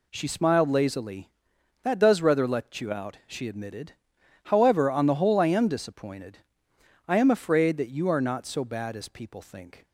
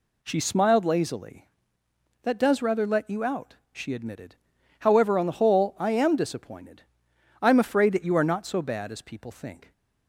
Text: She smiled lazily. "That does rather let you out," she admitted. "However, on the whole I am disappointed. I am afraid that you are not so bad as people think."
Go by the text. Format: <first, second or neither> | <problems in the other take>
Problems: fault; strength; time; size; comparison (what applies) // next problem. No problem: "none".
neither | none